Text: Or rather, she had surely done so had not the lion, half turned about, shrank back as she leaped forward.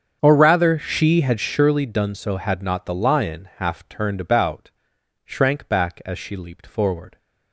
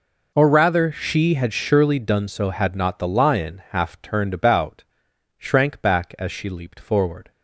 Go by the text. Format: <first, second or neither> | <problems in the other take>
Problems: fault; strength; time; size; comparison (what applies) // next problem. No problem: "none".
second | starts louder than the rest; strong; until 1.5 s; 7.5 dB